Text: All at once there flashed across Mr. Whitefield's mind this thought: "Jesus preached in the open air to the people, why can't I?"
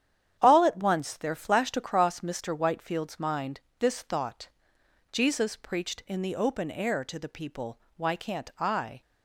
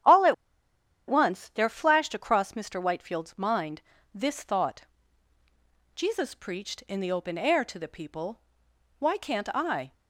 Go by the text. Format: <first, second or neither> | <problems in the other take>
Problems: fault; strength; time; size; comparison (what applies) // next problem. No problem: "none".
first | starts louder than the rest; strong; until 1.8 s; 9.5 dB; strong in the first // pauses between "at" and "once"; noticeable; at 0.3 s; 0.73 s long // pauses between "mind" and "this"; slight; at 3.8 s; 0.32 s long; slight in the first